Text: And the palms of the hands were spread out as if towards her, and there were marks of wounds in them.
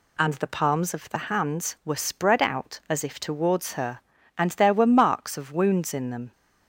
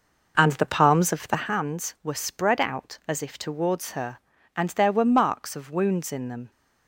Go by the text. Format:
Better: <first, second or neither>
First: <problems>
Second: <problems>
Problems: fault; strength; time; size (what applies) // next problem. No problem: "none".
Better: first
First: none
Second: starts louder than the rest; noticeable; until 1.6 s; 5.5 dB